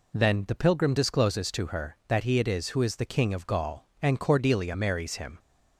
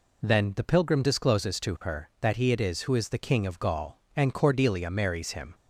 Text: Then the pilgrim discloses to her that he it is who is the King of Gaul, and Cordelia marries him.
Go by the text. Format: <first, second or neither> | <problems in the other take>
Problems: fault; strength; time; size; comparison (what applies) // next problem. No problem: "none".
neither | none